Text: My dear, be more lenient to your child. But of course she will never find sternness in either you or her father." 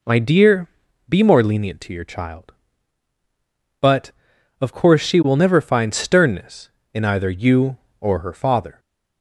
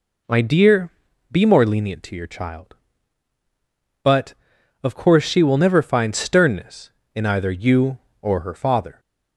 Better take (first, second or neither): neither